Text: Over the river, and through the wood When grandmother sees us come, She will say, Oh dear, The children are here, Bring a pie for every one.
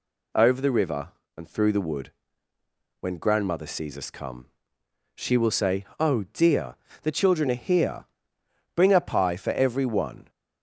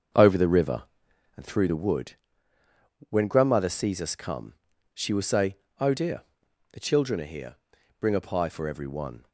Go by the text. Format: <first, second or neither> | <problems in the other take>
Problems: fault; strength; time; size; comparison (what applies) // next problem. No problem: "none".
first | starts louder than the rest; until 1.5 s; 6.5 dB // pauses between "wood" and "When"; noticeable; at 2.1 s; 0.96 s long; noticeable in the first